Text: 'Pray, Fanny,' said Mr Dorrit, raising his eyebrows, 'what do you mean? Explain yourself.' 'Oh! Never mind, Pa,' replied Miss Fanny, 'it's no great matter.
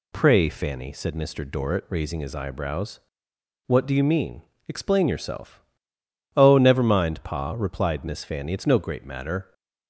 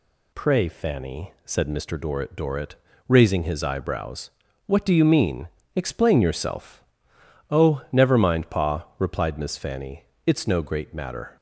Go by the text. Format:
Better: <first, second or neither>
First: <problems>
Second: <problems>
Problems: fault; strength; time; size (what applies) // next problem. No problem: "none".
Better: first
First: none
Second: says "Dorrit" twice; at 2.3 s